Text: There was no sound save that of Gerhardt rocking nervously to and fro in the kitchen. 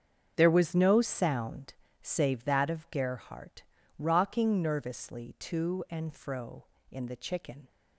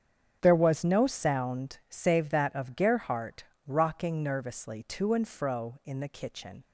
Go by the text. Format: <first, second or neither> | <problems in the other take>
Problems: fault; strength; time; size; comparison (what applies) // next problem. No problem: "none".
second | starts louder than the rest; until 1.3 s; 7 dB; strong in the second // pauses between "sound" and "save"; slight; at 1.7 s; 0.30 s long // pauses between "Gerhardt" and "rocking"; slight; at 3.6 s; 0.36 s long; slight in the second // says "chicken" for "kitchen"; at 7.1 s